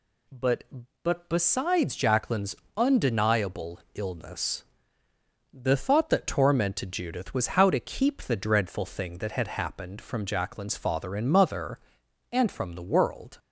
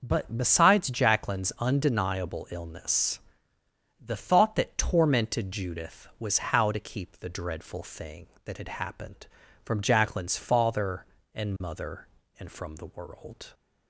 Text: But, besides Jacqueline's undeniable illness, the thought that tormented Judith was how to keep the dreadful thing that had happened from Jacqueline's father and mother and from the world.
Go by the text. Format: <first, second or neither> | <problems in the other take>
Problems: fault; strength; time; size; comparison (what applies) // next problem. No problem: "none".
second | says "But" twice; at 1.0 s // pauses between "Jacqueline's" and "undeniable"; slight; at 2.5 s; 0.22 s long